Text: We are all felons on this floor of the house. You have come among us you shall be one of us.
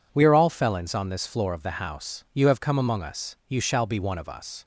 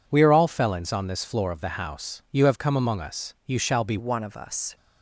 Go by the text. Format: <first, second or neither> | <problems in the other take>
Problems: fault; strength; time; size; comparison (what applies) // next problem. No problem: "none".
first | changes voice at "one"; from 3.9 s on; 0.8 s long